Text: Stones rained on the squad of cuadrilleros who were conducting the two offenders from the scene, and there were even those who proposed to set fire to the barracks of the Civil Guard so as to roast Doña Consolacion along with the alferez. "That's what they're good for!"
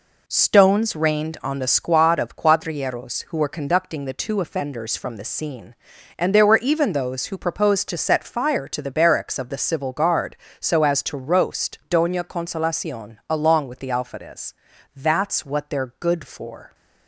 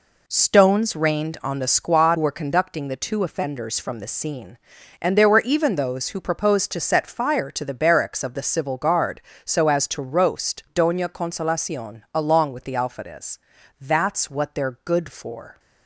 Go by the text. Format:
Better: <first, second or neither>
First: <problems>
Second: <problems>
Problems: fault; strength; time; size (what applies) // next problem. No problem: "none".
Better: first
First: none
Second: skips "of cuadrilleros who"; at 2.1 s